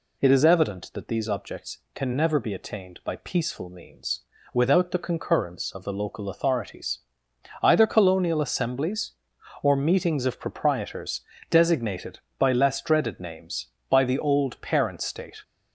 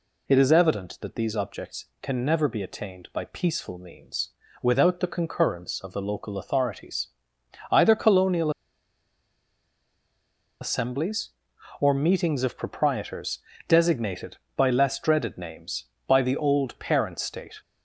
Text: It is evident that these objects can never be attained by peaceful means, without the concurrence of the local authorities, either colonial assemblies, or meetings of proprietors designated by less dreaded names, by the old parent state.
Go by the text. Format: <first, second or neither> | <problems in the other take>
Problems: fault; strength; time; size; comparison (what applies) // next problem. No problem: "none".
first | pauses between "colonial" and "assemblies"; strong; at 8.4 s; 2.1 s long // pauses between "proprietors" and "designated"; slight; at 13.4 s; 0.28 s long; slight in the first